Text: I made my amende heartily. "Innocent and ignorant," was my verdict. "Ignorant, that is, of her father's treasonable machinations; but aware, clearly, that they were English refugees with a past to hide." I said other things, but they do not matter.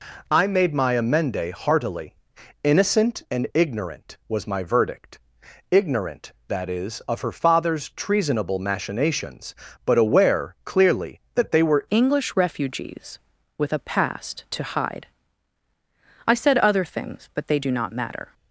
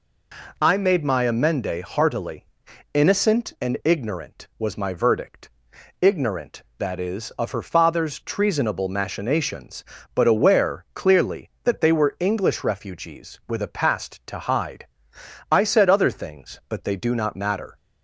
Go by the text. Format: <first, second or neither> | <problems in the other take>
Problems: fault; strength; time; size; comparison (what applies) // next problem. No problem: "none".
second | changes voice at "English"; from 11.8 s on; 6.5 s long